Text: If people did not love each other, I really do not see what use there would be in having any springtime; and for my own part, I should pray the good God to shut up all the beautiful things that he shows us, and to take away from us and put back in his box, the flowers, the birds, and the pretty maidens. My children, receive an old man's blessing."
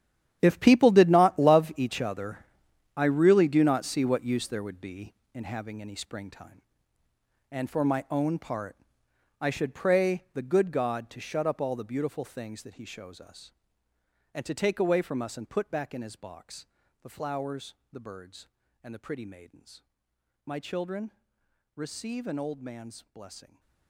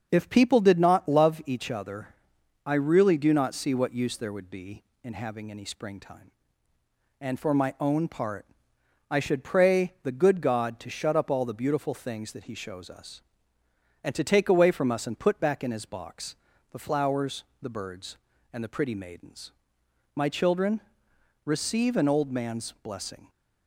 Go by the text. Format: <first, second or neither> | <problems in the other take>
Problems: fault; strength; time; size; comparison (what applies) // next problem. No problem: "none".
second | gets quieter; strong; throughout; 14.5 dB // starts louder than the rest; strong; until 1.4 s; 10.5 dB; also in the second